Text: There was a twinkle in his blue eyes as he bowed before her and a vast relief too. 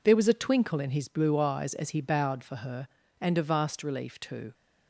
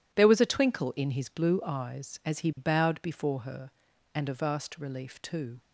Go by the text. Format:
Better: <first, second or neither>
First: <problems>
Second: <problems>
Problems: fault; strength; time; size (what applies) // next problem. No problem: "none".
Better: second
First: says "for" for "before"; at 2.4 s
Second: none